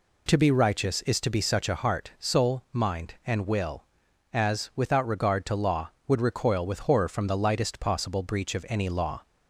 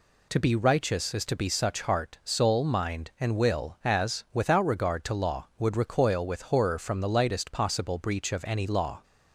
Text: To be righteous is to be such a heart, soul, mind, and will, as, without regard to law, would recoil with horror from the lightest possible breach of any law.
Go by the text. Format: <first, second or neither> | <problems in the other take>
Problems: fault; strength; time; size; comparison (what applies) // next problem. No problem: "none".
first | skips "a"; at 1.8 s